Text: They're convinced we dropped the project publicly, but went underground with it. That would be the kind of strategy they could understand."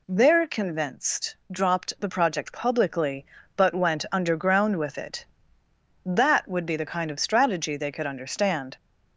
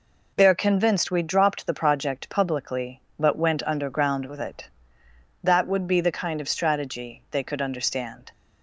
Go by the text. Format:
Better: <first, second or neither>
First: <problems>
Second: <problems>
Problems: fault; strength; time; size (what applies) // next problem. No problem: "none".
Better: second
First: skips "we"; at 1.4 s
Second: none